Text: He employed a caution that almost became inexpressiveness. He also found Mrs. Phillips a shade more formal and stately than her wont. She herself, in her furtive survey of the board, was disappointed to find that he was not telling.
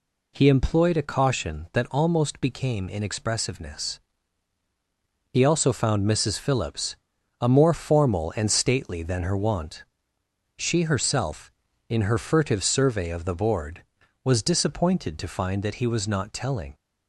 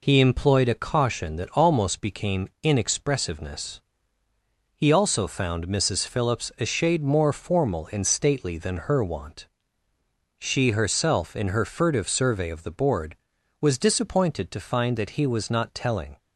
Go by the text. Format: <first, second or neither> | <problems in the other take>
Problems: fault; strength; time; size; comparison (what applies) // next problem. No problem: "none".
second | pauses between "Phillips" and "a"; at 6.9 s; 0.44 s long // skips "shade"; at 7.4 s